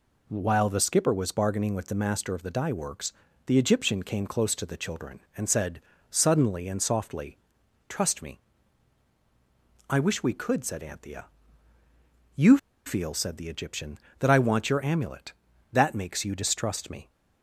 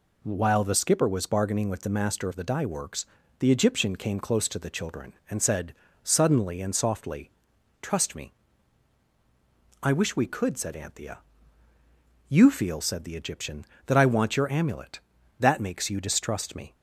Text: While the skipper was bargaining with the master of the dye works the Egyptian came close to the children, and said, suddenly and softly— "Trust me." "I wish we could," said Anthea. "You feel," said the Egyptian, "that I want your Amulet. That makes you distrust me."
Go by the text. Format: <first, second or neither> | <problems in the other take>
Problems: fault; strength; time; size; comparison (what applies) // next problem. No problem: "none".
second | pauses between "works" and "the"; slight; at 3.1 s; 0.32 s long; slight in the second // pauses between "You" and "feel"; slight; at 12.5 s; 0.28 s long